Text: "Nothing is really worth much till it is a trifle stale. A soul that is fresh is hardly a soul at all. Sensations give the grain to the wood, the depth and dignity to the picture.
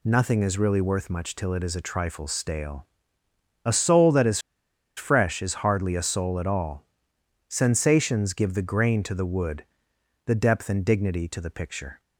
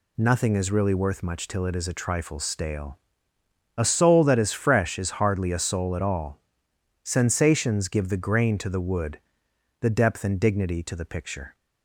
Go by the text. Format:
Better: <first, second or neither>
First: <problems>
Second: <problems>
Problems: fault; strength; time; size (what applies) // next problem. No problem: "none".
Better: second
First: pauses between "is" and "fresh"; noticeable; at 4.3 s; 0.56 s long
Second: none